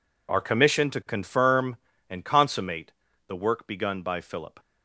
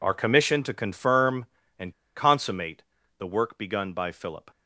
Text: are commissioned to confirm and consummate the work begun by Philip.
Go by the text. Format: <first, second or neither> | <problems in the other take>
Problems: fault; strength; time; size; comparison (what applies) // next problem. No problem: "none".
first | pauses between "and" and "consummate"; slight; at 1.9 s; 0.22 s long // pauses between "consummate" and "the"; slight; at 2.8 s; 0.36 s long; slight in the first